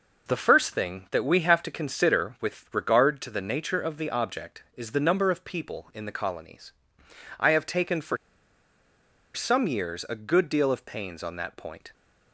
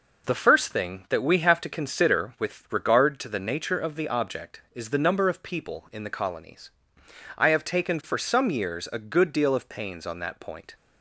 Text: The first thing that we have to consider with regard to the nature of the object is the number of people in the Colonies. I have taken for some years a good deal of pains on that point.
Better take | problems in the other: second | pauses between "for" and "some"; at 8.1 s; 1.1 s long

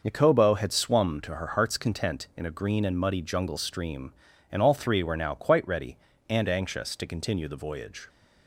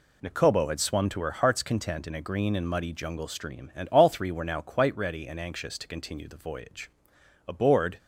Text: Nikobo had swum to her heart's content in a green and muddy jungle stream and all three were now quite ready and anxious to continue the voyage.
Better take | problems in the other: first | goes on to say "Aboard"; from 7.4 s on; 0.52 s long

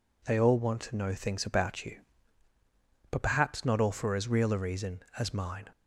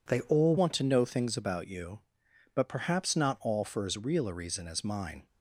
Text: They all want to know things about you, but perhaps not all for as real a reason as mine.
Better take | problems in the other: first | changes voice at "want"; from 0.5 s on; 4.7 s long

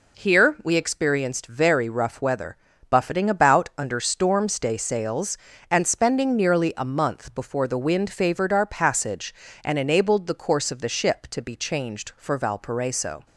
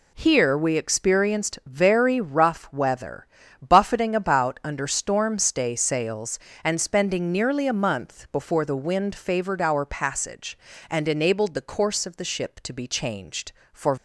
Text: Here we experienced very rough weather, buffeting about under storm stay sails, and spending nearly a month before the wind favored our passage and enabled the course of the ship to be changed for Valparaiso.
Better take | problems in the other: first | stops before "Valparaiso"; at 13.9 s

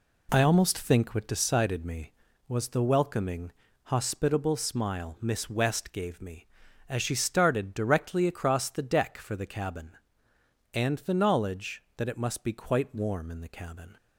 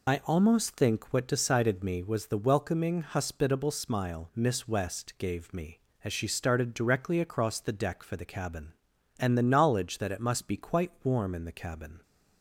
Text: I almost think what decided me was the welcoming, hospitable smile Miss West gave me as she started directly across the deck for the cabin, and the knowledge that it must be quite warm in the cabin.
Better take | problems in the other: first | loses the start of "I"; at 0.0 s; 45 ms

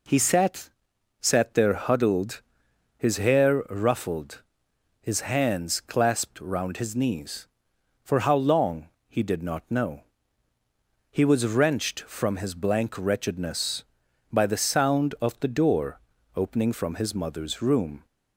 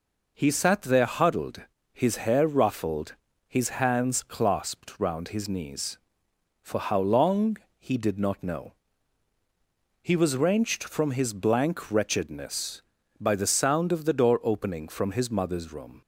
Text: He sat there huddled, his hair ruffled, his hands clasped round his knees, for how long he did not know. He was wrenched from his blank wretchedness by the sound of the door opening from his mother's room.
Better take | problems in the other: second | says "sat" twice; at 1.1 s // pauses between "long" and "he"; slight; at 8.8 s; 0.22 s long; slight in the second // pauses between "door" and "opening"; at 15.9 s; 0.38 s long

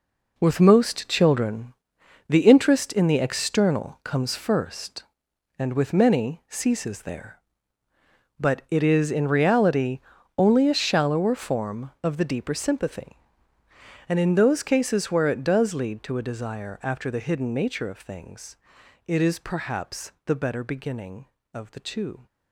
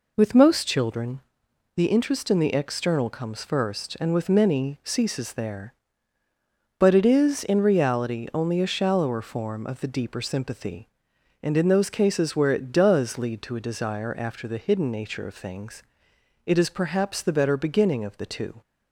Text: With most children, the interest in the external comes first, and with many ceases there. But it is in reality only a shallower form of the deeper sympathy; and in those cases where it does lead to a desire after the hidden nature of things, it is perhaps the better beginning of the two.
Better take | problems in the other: second | gets quieter; strong; throughout; 10 dB // pauses between "reality" and "only"; slight; at 10.0 s; 0.36 s long

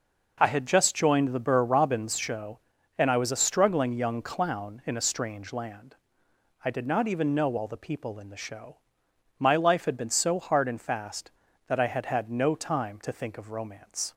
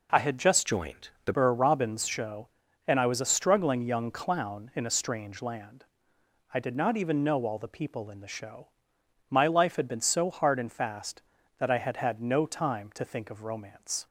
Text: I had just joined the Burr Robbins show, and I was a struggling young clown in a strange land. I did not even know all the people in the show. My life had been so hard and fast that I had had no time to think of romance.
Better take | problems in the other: first | changes voice from "joined" to "the"; from 0.6 to 1.3 s; 0.7 s long

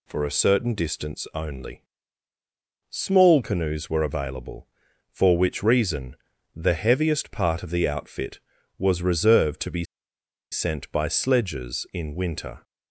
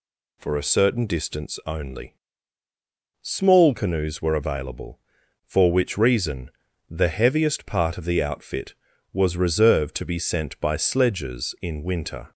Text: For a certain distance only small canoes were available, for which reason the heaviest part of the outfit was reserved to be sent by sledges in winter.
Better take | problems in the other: second | pauses between "only" and "small"; at 1.8 s; 1.0 s long; also in the second // pauses between "reason" and "the"; at 6.1 s; 0.40 s long; also in the second // pauses between "be" and "sent"; noticeable; at 9.8 s; 0.68 s long

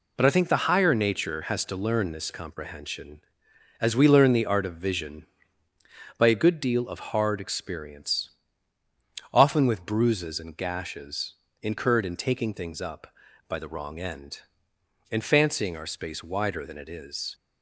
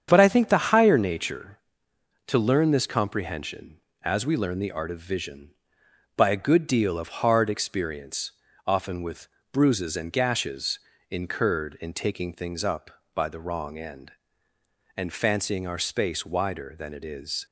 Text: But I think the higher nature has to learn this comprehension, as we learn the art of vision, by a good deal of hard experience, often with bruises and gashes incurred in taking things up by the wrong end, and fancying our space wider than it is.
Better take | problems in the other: first | starts louder than the rest; strong; until 1.1 s; 8 dB // skips "has"; at 1.9 s // pauses between "with" and "bruises"; slight; at 9.2 s; 0.24 s long // pauses between "gashes" and "incurred"; slight; at 10.7 s; 0.32 s long; slight in the first

